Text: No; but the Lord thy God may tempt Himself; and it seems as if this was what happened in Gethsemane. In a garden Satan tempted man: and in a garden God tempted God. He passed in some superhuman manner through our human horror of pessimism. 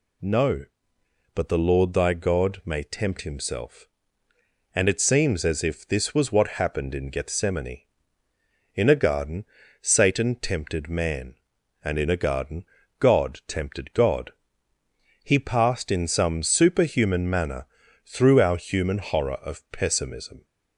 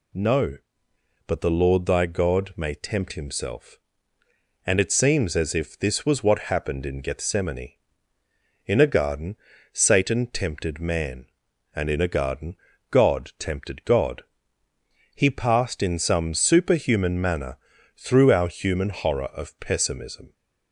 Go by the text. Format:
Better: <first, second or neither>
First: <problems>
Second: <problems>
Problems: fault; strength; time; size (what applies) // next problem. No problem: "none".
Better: neither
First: pauses between "garden" and "Satan"; at 9.4 s; 0.38 s long // pauses between "garden" and "God"; slight; at 12.6 s; 0.34 s long // pauses between "manner" and "through"; at 17.6 s; 0.40 s long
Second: pauses between "garden" and "Satan"; at 9.3 s; 0.38 s long // pauses between "garden" and "God"; slight; at 12.5 s; 0.34 s long // pauses between "manner" and "through"; at 17.5 s; 0.40 s long